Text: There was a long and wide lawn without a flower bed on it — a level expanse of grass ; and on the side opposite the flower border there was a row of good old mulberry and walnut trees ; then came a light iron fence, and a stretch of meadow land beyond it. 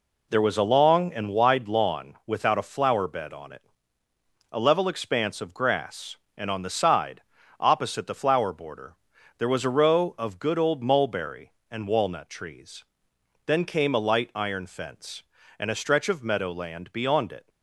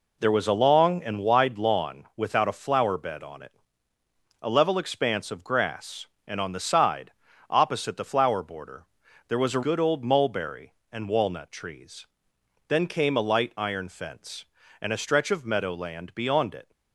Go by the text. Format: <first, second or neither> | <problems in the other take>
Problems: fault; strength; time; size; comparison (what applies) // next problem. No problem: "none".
first | pauses between "side" and "opposite"; at 7.1 s; 0.38 s long; also in the first // pauses between "border" and "there"; at 8.8 s; 0.44 s long; also in the first // skips "row of"; at 9.6 s